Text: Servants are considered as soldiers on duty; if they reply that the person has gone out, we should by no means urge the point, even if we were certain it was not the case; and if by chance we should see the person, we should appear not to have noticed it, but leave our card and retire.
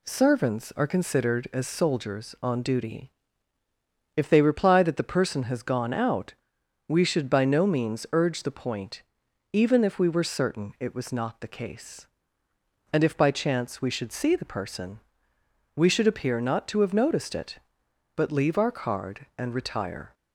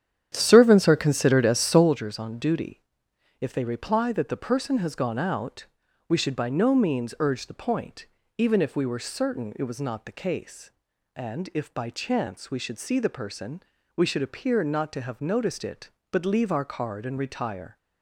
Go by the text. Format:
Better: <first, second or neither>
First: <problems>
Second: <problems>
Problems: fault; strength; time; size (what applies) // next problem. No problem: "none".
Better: first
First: none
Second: starts louder than the rest; strong; until 2.0 s; 9.5 dB